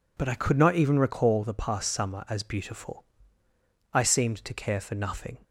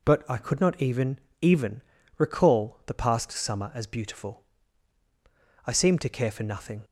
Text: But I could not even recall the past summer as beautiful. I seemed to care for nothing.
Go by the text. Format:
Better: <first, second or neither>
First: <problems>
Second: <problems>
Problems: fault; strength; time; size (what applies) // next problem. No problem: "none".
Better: first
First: none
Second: says "even" twice; at 1.3 s